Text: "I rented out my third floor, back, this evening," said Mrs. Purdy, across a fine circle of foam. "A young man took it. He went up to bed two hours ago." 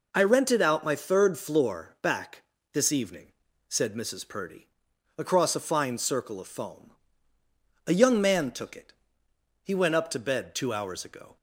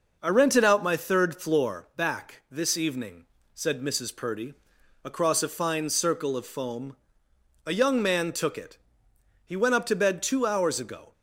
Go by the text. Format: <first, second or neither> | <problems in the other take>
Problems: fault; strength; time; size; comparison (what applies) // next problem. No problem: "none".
neither | none